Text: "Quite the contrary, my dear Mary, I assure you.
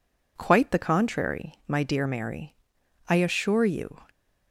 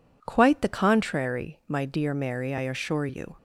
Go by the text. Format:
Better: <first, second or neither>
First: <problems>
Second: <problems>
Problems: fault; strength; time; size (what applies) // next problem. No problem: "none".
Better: neither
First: none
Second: none